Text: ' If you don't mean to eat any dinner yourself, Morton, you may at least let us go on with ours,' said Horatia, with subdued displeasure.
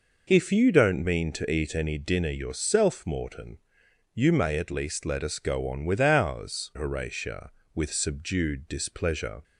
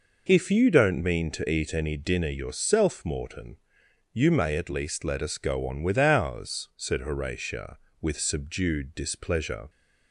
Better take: second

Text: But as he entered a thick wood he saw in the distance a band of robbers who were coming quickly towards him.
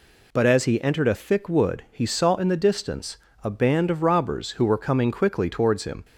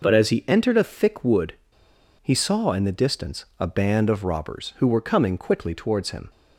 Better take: first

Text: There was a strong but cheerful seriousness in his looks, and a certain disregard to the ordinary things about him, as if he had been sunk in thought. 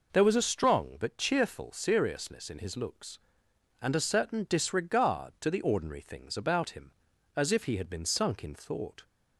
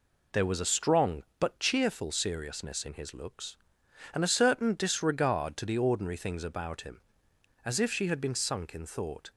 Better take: first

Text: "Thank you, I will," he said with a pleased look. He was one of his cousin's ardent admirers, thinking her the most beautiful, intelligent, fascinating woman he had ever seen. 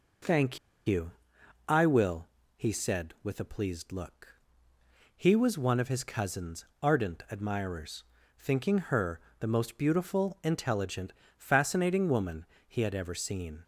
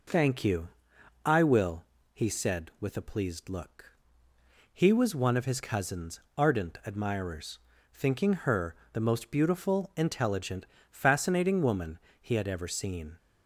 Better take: second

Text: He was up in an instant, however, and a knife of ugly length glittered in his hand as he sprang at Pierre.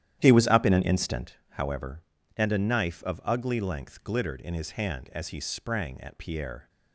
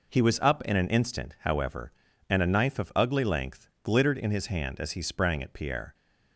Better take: second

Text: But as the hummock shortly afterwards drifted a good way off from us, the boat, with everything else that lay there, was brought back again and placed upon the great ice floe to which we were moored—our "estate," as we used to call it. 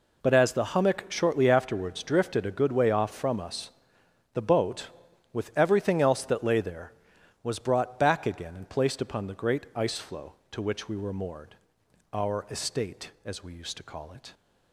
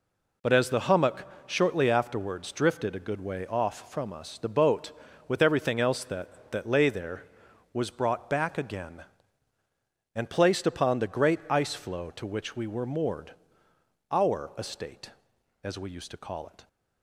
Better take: first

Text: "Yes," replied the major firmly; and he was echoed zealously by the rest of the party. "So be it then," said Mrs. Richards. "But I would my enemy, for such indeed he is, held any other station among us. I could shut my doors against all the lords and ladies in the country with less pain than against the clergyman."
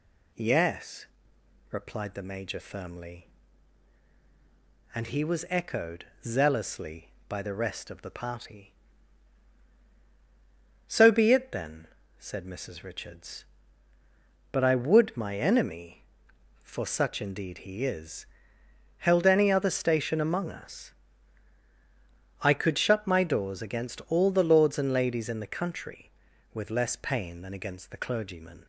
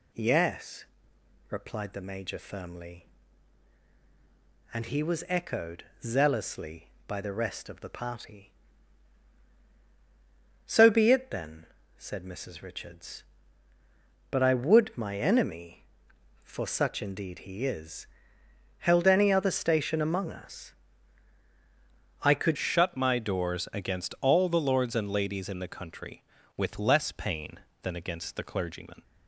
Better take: first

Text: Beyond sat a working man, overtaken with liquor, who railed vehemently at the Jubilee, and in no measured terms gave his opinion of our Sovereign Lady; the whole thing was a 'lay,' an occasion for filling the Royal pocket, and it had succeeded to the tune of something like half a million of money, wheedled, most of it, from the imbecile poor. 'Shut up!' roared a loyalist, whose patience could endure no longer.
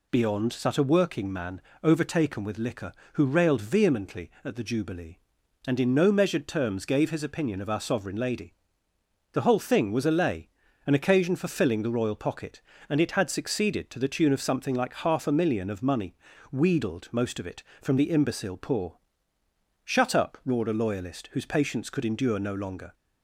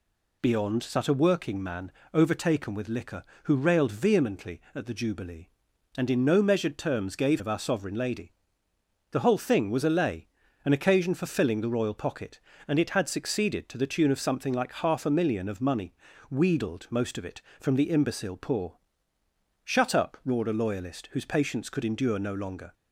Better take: first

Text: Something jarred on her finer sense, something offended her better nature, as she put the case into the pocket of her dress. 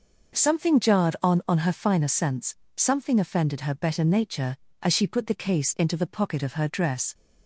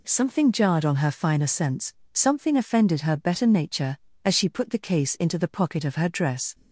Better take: second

